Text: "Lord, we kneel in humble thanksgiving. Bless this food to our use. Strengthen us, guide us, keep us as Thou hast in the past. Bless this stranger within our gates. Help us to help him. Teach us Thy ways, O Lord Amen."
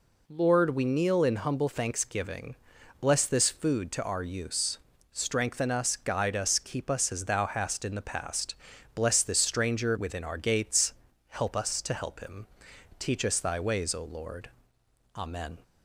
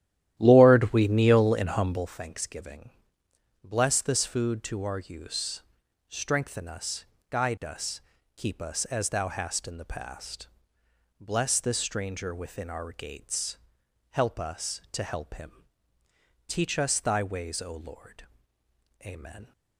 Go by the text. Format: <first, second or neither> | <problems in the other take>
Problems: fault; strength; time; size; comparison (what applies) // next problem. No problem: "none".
first | starts louder than the rest; strong; until 2.1 s; 12.5 dB // pauses between "Lord" and "Amen"; noticeable; at 18.2 s; 0.80 s long; noticeable in the first